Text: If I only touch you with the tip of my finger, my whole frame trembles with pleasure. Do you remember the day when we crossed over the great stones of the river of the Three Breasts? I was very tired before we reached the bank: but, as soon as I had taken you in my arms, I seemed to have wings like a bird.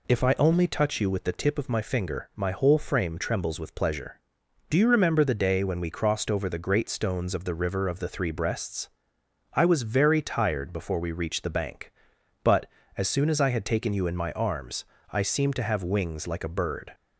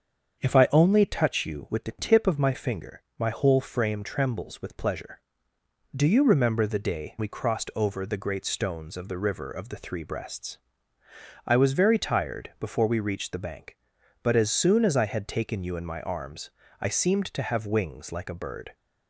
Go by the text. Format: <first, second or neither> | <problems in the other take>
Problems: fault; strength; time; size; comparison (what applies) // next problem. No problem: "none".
first | starts louder than the rest; strong; until 1.4 s; 7 dB // skips "when"; at 7.1 s